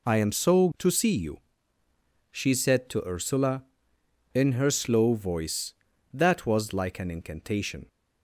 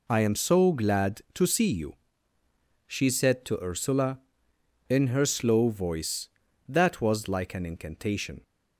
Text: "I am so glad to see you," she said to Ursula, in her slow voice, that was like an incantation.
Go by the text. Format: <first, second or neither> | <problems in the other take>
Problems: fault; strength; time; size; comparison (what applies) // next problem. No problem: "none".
second | skips "glad"; at 0.7 s